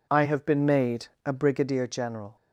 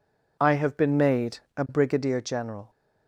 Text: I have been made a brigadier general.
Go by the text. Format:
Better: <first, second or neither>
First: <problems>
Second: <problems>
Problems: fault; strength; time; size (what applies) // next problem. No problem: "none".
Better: neither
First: pauses between "made" and "a"; slight; at 1.0 s; 0.16 s long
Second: pauses between "made" and "a"; slight; at 1.3 s; 0.16 s long